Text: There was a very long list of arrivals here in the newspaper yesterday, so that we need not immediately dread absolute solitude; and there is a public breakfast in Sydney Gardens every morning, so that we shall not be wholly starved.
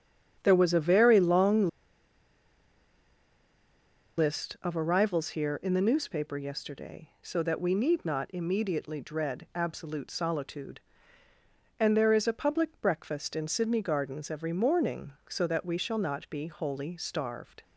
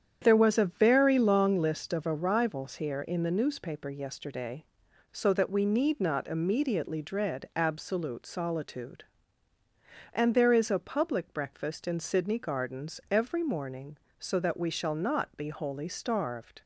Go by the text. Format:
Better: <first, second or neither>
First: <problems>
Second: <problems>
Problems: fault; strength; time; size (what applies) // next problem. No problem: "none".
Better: second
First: starts louder than the rest; strong; until 1.4 s; 8.5 dB // pauses between "long" and "list"; strong; at 1.6 s; 2.5 s long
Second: starts louder than the rest; strong; until 1.2 s; 8.5 dB